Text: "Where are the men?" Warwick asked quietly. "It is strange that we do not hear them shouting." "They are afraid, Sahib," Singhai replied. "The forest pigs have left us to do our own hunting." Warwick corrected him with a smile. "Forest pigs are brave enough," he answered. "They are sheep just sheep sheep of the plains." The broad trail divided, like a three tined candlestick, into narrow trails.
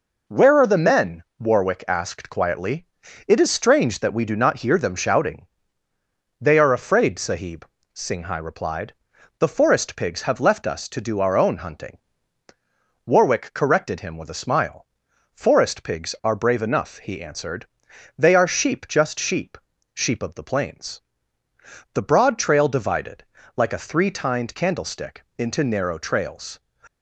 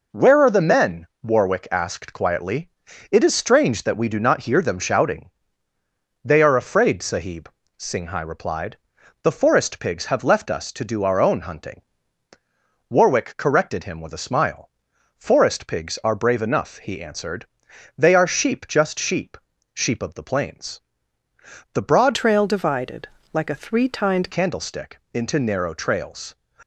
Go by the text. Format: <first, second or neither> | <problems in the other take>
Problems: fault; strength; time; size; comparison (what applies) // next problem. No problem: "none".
first | pauses between "sheep" and "sheep"; at 19.3 s; 0.38 s long; also in the first // changes voice from "trail" to "tined"; from 22.1 to 24.2 s; 2.1 s long